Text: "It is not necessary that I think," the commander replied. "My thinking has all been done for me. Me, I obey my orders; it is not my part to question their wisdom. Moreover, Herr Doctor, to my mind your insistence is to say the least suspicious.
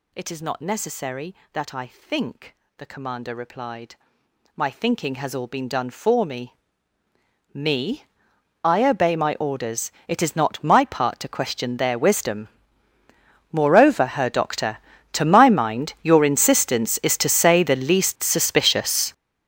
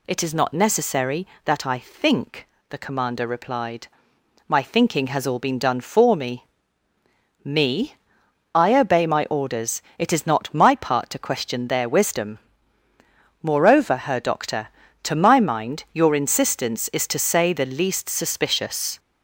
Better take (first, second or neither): second